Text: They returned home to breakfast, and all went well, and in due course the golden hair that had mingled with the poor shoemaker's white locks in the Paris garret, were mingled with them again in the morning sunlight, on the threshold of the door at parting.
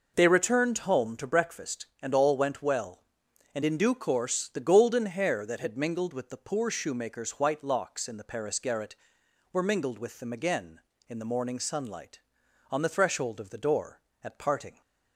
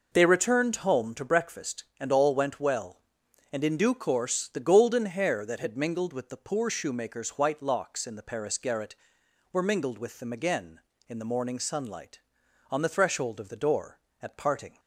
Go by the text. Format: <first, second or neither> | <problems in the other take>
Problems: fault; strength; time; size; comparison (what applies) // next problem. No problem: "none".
neither | none